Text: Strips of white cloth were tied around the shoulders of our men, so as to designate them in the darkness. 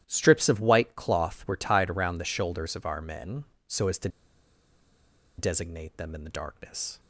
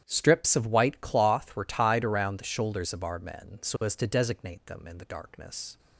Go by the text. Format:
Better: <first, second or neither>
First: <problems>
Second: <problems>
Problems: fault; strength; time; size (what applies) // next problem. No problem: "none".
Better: second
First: starts louder than the rest; strong; until 1.0 s; 12.5 dB // pauses between "to" and "designate"; strong; at 4.0 s; 1.3 s long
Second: starts louder than the rest; strong; until 1.0 s; 10.5 dB